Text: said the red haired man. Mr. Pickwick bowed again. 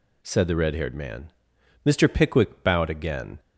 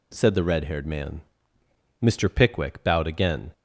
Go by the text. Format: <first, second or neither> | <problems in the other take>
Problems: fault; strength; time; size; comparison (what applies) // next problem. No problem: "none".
neither | none